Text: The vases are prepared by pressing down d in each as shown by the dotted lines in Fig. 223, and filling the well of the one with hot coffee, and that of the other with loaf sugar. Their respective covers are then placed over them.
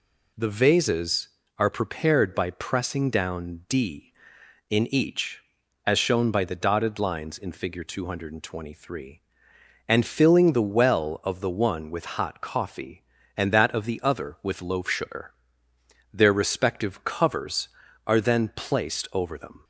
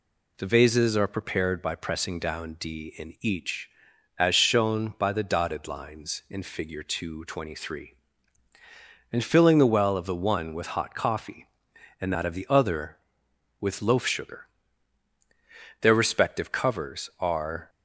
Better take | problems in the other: first | stops before "then placed over them"; at 17.6 s

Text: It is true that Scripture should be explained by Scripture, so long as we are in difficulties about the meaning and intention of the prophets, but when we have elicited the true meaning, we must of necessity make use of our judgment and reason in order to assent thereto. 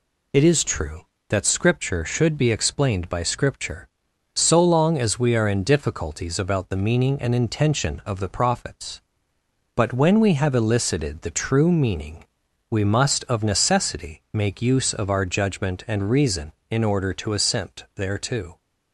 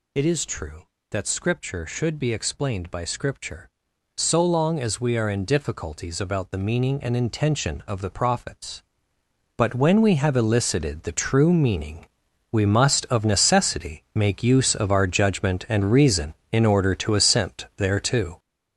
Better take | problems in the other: first | gets louder; strong; throughout; 7.5 dB

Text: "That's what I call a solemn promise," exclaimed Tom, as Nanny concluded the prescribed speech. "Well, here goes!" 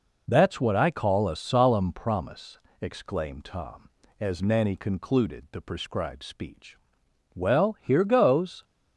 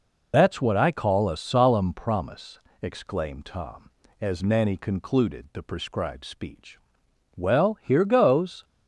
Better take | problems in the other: first | loses the start of "That's"; at 0.3 s; 55 ms

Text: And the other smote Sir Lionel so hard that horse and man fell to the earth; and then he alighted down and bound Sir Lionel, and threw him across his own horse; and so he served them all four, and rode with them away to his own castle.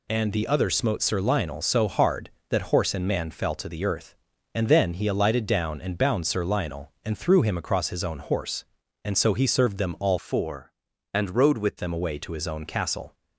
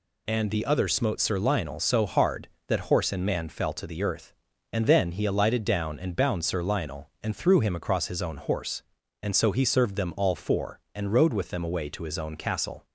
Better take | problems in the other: second | changes voice from "four" to "with"; from 10.1 to 11.7 s; 1.6 s long

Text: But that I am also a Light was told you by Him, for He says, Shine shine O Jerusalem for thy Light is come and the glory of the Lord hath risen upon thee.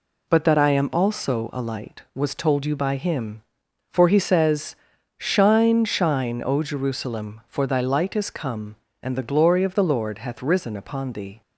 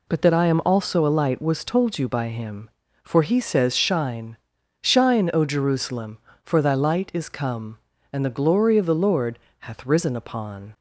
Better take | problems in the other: first | pauses between "Shine" and "shine"; at 4.3 s; 0.44 s long // pauses between "Lord" and "hath"; slight; at 9.3 s; 0.28 s long // stops before "thee"; at 10.7 s

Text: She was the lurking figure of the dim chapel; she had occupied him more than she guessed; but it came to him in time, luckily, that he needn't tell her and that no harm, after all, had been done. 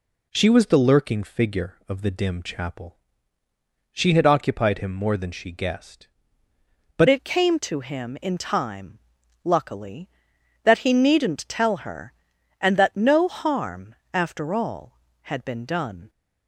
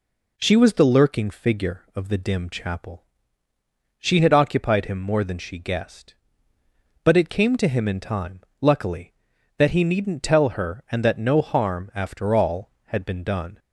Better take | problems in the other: second | changes voice at "it"; from 7.0 s on; 9.0 s long

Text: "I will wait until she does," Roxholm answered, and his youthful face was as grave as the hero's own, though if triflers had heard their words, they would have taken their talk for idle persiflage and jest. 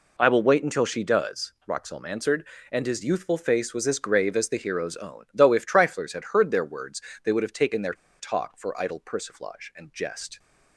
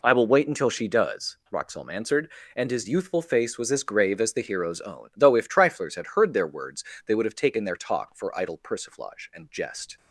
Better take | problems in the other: second | pauses between "their" and "talk"; slight; at 7.9 s; 0.26 s long

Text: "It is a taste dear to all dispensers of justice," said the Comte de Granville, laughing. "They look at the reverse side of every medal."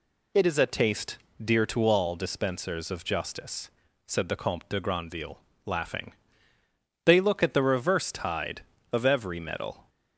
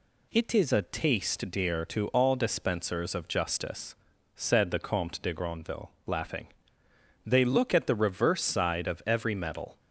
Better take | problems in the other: second | pauses between "taste" and "dear"; slight; at 1.1 s; 0.26 s long // says "tide" for "side"; at 8.1 s

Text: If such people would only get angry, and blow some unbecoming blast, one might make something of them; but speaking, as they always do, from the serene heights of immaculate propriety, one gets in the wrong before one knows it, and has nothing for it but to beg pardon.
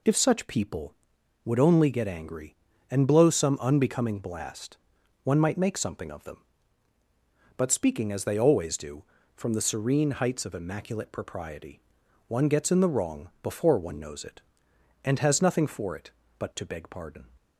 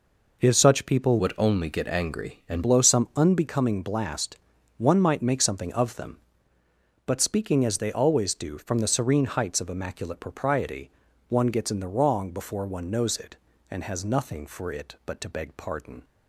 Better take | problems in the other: first | changes voice from "would" to "and"; from 1.1 to 2.6 s; 1.5 s long

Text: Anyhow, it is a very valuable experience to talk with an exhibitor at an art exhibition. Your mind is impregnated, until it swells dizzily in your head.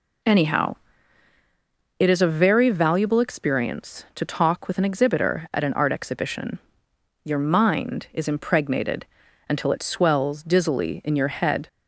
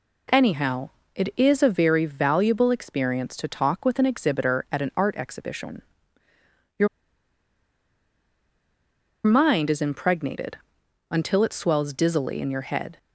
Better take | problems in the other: first | pauses between "Your" and "mind"; strong; at 6.8 s; 2.3 s long

